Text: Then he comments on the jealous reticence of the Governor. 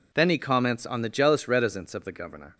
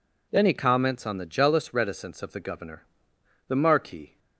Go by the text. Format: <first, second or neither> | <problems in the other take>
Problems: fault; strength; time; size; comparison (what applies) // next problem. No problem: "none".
first | goes on to say "The Marquis"; noticeable; from 3.4 s on; 0.72 s long